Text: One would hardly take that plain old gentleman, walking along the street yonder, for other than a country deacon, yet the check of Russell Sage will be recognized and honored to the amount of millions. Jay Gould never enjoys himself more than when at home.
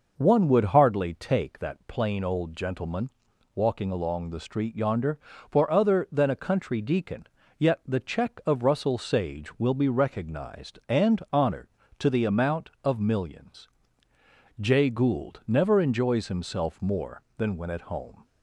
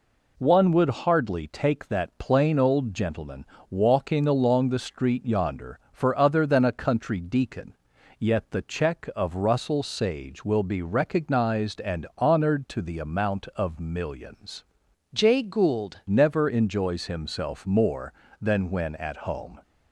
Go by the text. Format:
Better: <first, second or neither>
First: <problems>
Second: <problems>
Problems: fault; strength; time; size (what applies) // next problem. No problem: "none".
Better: first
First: none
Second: changes voice from "Jay" to "Gould"; from 15.1 to 15.9 s; 0.8 s long